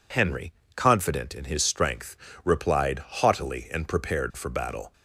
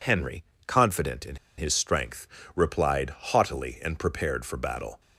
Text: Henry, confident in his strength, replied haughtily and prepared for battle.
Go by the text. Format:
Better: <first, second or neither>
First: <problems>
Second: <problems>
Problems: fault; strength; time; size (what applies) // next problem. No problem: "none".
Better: first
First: none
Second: pauses between "in" and "his"; slight; at 1.3 s; 0.21 s long